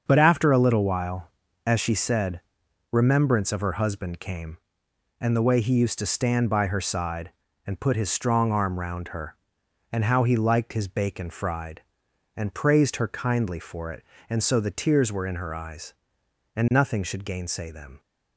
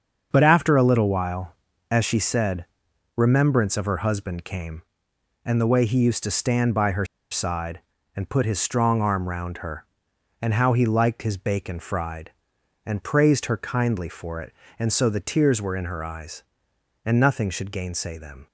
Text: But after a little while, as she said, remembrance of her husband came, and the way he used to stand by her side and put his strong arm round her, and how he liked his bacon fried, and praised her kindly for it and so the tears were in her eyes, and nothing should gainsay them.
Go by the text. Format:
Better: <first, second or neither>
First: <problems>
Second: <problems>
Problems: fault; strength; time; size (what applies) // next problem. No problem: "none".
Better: first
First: starts louder than the rest; until 1.0 s; 7 dB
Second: starts louder than the rest; until 1.3 s; 6.5 dB // pauses between "her" and "side"; slight; at 7.0 s; 0.27 s long